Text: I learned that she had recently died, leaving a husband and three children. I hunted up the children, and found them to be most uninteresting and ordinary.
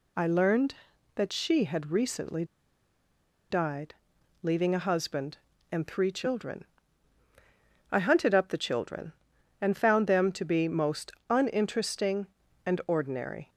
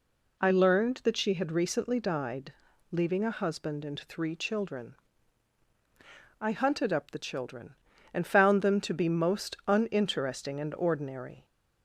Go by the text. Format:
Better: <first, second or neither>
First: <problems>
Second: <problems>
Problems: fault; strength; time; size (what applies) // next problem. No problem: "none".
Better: second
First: pauses between "recently" and "died"; at 2.4 s; 1.0 s long // pauses between "most" and "uninteresting"; slight; at 11.1 s; 0.16 s long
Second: none